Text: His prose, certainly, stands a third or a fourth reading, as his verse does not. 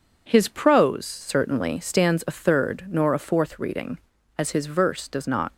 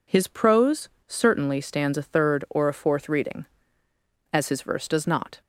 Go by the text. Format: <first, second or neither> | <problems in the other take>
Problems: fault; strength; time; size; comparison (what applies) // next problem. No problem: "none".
second | says "nor" for "or"; at 2.8 s